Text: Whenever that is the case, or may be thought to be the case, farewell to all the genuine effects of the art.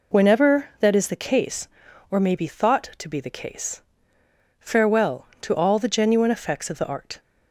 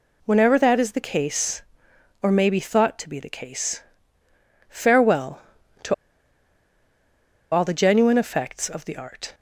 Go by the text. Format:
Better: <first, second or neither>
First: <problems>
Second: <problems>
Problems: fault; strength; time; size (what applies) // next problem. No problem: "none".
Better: first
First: none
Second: pauses between "to" and "all"; strong; at 5.9 s; 1.5 s long